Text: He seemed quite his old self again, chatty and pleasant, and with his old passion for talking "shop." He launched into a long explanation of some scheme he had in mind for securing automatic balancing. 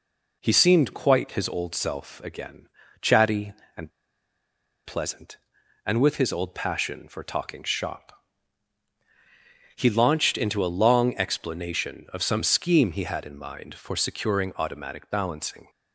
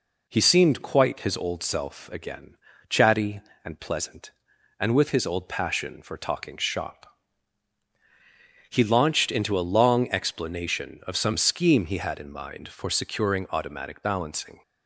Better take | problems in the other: second | pauses between "and" and "pleasant"; noticeable; at 3.9 s; 0.94 s long

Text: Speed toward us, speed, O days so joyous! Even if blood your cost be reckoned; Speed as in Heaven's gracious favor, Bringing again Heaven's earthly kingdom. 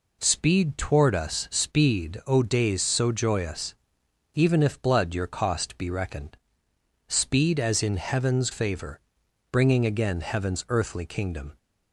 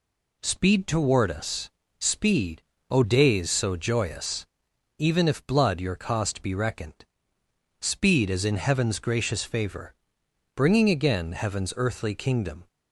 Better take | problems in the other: second | skips "gracious"; at 8.5 s

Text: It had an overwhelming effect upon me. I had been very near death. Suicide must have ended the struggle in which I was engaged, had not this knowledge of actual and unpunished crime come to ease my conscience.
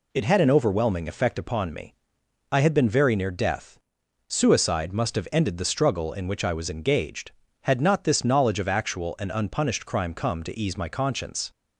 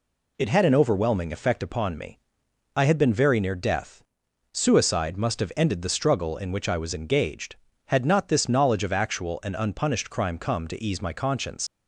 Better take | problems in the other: first | leaves "conscience" unfinished; at 11.6 s; 100 ms

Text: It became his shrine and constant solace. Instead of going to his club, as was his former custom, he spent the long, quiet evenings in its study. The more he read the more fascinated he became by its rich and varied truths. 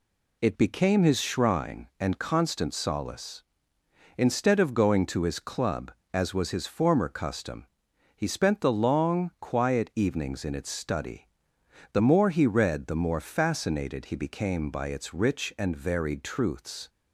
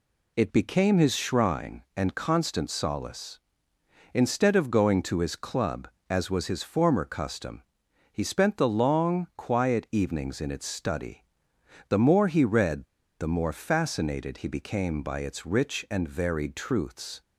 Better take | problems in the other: first | pauses between "read" and "the"; slight; at 12.8 s; 0.36 s long

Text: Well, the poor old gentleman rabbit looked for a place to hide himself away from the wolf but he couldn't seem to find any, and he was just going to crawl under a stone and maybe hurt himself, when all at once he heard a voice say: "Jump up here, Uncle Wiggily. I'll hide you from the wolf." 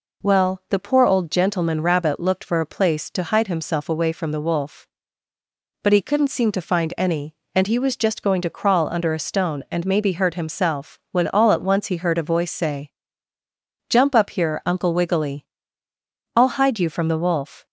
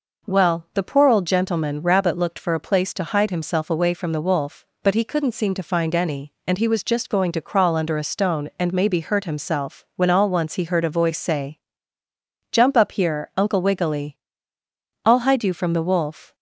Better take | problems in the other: first | skips "at"; at 10.2 s

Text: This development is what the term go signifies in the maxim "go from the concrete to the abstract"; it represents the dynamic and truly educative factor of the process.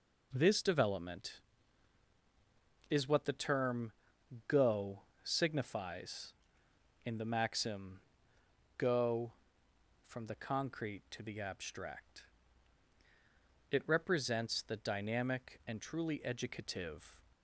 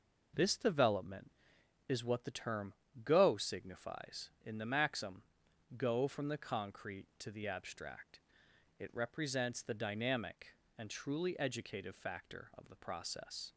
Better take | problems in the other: second | pauses between "term" and "go"; noticeable; at 3.9 s; 0.56 s long; slight in the second // pauses between "go" and "signifies"; slight; at 5.0 s; 0.24 s long // pauses between "maxim" and "go"; noticeable; at 7.9 s; 0.80 s long; noticeable in the second // stops before "factor of the process"; at 17.3 s

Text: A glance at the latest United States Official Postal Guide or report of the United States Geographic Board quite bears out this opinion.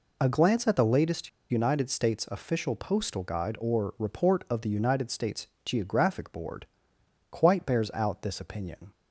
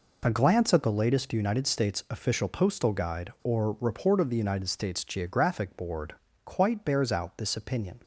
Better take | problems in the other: second | pauses between "latest" and "United"; slight; at 1.2 s; 0.24 s long // pauses between "States" and "Geographic"; slight; at 5.4 s; 0.18 s long // pauses between "Board" and "quite"; noticeable; at 6.6 s; 0.66 s long; slight in the second

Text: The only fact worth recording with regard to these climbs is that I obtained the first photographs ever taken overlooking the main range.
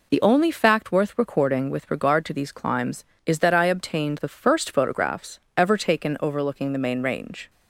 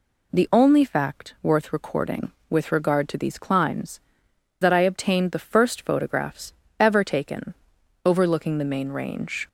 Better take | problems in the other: first | skips "is"; at 4.2 s // pauses between "photographs" and "ever"; slight; at 6.5 s; 0.26 s long; slight in the first // pauses between "taken" and "overlooking"; noticeable; at 7.5 s; 0.50 s long

